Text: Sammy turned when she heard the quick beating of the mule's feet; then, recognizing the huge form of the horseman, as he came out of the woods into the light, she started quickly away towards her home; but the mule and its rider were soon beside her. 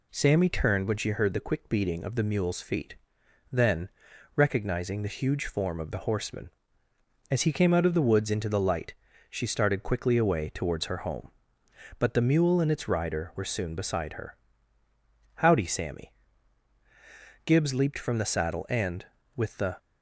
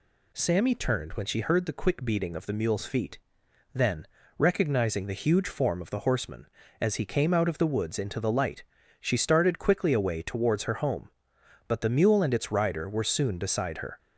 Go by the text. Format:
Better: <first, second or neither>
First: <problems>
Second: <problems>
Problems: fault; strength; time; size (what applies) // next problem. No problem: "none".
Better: second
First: goes on to say "Howdy Sammy Gibbs leaped from the saddle and with the"; strong; from 15.3 s on; 4.4 s long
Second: none